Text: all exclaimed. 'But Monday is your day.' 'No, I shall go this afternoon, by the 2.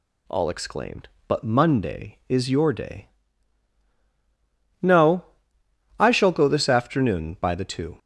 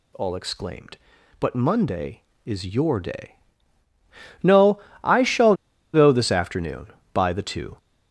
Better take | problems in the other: first | pauses between "shall" and "go"; at 5.5 s; 0.39 s long

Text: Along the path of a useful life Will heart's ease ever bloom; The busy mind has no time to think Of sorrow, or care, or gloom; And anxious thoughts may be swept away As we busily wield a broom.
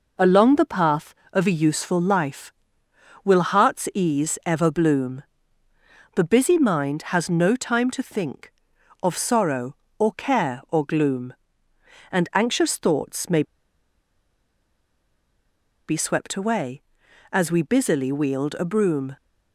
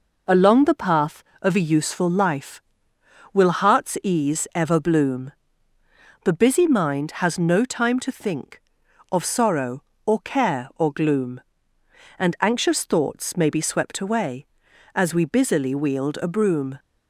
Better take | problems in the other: second | pauses between "may" and "be"; strong; at 13.4 s; 2.4 s long

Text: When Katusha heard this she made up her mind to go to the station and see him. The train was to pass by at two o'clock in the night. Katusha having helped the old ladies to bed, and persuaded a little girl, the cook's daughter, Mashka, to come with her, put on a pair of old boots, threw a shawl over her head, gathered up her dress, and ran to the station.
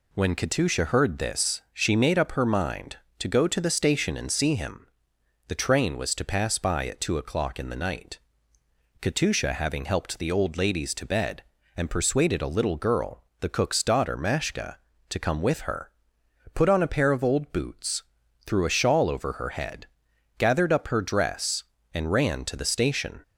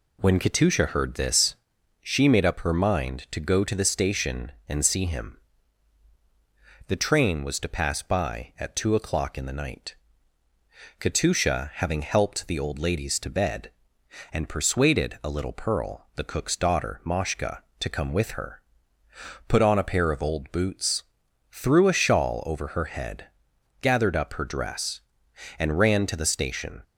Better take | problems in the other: first | pauses between "this" and "she"; noticeable; at 1.5 s; 0.46 s long // says "pearl" for "girl"; at 15.5 s

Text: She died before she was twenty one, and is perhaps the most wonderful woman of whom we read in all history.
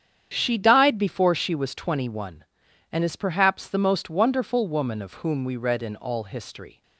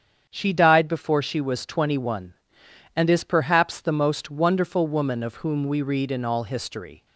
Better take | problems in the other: neither | starts louder than the rest; strong; the same in both

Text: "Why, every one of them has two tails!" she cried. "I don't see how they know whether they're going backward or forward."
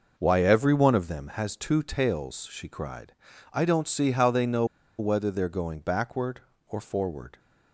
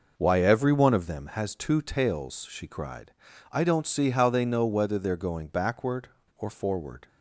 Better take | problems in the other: second | pauses between "know" and "whether"; slight; at 4.6 s; 0.34 s long

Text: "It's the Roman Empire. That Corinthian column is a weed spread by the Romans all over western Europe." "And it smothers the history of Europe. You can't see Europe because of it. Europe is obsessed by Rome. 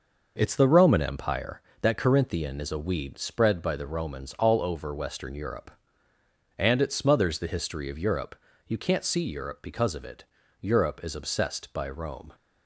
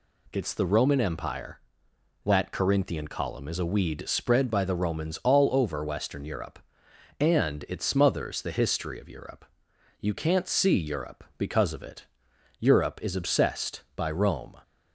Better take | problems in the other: second | skips "column"; at 2.6 s

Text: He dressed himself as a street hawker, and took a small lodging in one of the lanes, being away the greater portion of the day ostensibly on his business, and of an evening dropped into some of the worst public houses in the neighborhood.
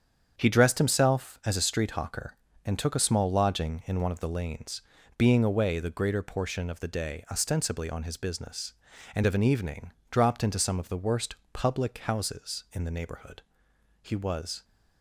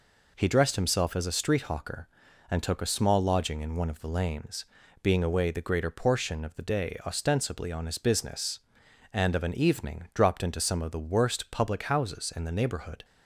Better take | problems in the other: second | starts louder than the rest; strong; until 1.3 s; 7.5 dB // pauses between "evening" and "dropped"; slight; at 9.9 s; 0.18 s long // pauses between "worst" and "public"; slight; at 11.3 s; 0.18 s long // goes on to say "He was"; noticeable; from 14.0 s on; 0.62 s long

